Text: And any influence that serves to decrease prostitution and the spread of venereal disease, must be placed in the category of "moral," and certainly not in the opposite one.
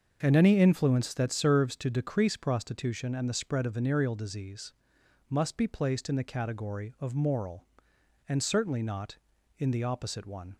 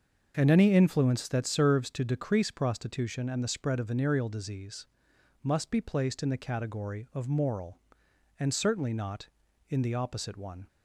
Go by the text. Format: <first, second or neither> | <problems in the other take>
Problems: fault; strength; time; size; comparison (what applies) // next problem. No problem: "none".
neither | starts louder than the rest; the same in both